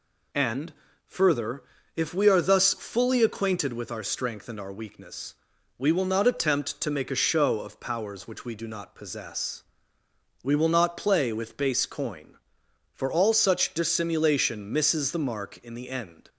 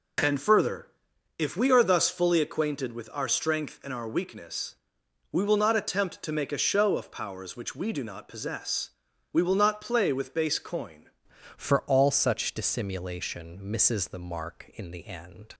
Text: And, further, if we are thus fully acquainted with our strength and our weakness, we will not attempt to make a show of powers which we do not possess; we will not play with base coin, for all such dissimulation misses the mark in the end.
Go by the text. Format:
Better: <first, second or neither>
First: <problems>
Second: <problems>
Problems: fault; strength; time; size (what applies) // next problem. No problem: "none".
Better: first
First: none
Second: changes voice at "for"; from 11.5 s on; 4.0 s long